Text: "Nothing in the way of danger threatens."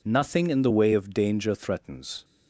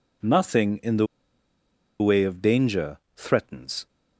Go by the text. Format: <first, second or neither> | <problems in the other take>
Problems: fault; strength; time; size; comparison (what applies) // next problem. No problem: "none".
first | pauses between "the" and "way"; noticeable; at 1.0 s; 0.93 s long // pauses between "danger" and "threatens"; slight; at 2.9 s; 0.18 s long